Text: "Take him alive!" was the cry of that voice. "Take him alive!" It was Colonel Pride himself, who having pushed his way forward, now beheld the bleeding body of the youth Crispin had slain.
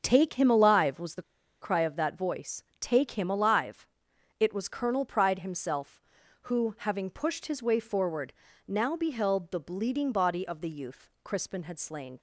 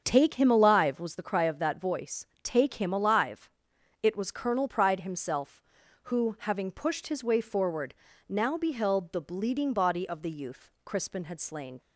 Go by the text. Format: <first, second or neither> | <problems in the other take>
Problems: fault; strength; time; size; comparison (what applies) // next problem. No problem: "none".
second | starts louder than the rest; strong; until 1.0 s; 7 dB; strong in the second // pauses between "the" and "cry"; at 1.2 s; 0.39 s long // pauses between "youth" and "Crispin"; slight; at 11.0 s; 0.16 s long; slight in the second